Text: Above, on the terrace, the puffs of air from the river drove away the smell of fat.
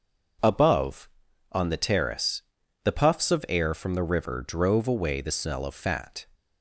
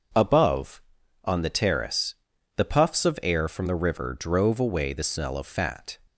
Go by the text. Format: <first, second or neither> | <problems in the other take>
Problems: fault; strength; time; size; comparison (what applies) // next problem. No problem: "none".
neither | none